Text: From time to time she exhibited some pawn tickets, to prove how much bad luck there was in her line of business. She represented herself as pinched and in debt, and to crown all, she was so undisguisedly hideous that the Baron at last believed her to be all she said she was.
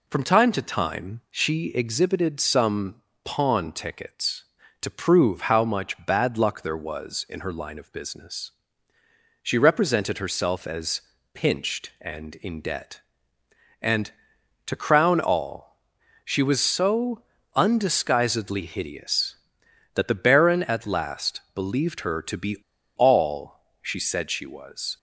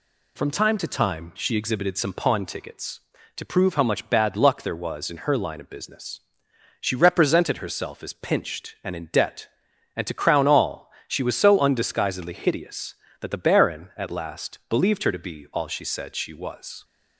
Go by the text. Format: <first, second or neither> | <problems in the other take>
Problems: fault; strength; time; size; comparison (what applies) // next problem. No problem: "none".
second | pauses between "some" and "pawn"; slight; at 3.0 s; 0.22 s long // pauses between "as" and "pinched"; slight; at 11.0 s; 0.32 s long // pauses between "so" and "undisguisedly"; slight; at 17.2 s; 0.32 s long // pauses between "be" and "all"; at 22.5 s; 0.41 s long // pauses between "all" and "she"; slight; at 23.5 s; 0.20 s long